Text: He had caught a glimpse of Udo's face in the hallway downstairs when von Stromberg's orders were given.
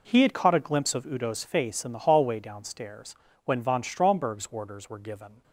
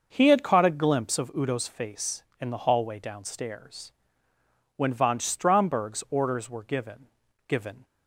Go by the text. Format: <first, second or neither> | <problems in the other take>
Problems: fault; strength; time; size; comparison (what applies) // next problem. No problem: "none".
first | starts louder than the rest; noticeable; until 1.1 s; 6 dB // pauses between "downstairs" and "when"; noticeable; at 3.9 s; 0.82 s long; slight in the first // says "given" twice; at 7.4 s